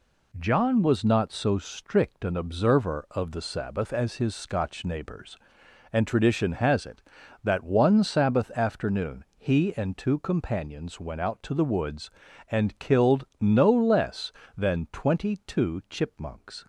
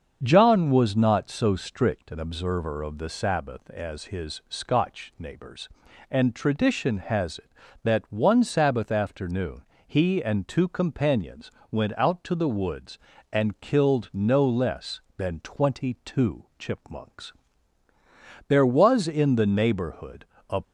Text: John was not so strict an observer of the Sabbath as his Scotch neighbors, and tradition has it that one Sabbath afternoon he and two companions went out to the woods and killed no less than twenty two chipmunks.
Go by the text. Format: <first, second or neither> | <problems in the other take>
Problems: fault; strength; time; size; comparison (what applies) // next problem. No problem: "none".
first | starts louder than the rest; until 1.2 s; 7 dB // pauses between "afternoon" and "he"; slight; at 9.6 s; 0.26 s long // pauses between "companions" and "went"; slight; at 11.4 s; 0.22 s long // goes on to say "There was in the neighborhood a"; strong; from 18.4 s on; 2.1 s long